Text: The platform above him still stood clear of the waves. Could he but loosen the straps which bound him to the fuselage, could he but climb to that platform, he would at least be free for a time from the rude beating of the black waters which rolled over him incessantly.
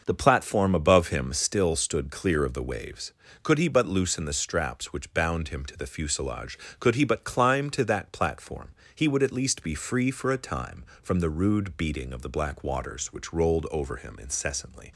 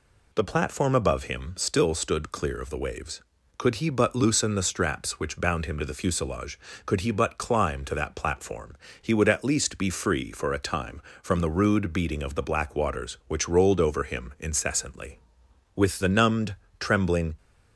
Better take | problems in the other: first | goes on to say "With the numbed trembling"; from 15.7 s on; 1.6 s long

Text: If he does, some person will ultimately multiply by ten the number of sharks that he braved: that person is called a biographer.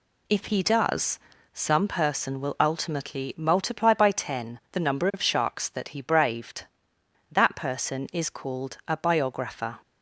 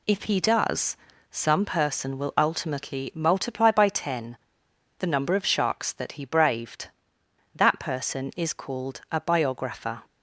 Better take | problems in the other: first | pauses between "ten" and "the"; noticeable; at 4.3 s; 0.61 s long

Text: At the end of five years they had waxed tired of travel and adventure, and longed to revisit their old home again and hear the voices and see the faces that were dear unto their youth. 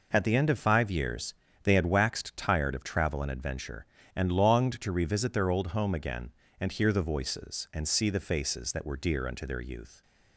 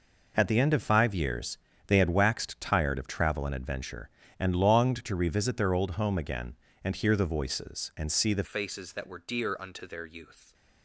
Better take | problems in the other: first | pauses between "years" and "they"; slight; at 1.5 s; 0.30 s long; slight in the first // changes voice at "faces"; from 8.4 s on; 2.1 s long

